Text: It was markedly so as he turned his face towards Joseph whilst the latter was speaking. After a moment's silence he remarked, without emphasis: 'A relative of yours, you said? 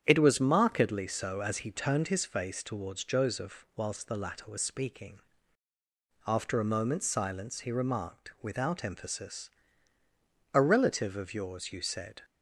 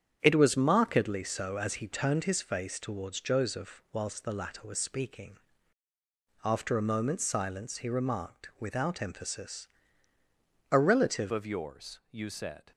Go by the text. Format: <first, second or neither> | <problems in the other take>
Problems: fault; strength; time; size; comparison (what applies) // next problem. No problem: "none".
first | starts louder than the rest; strong; until 1.2 s; 8.5 dB; strong in the first // changes voice at "of"; from 11.3 s on; 1.4 s long